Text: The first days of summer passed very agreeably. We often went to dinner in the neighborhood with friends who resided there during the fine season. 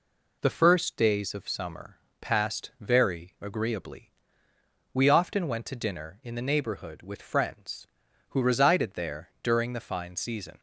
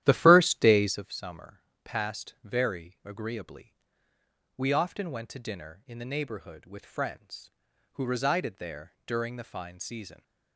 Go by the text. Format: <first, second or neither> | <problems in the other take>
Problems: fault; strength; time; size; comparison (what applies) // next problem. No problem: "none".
first | starts louder than the rest; strong; until 1.0 s; 12.5 dB // pauses between "summer" and "passed"; slight; at 1.6 s; 0.24 s long; slight in the first